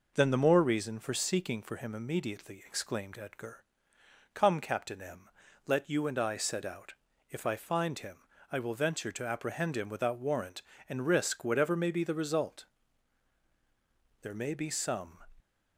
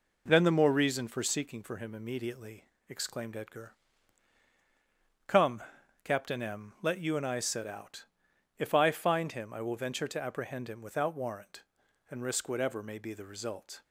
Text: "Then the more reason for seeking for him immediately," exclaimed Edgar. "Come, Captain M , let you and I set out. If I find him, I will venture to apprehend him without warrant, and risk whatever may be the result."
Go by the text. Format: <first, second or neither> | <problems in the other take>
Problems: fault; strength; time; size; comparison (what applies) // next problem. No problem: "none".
second | goes on to say "There may be some"; noticeable; from 14.2 s on; 1.0 s long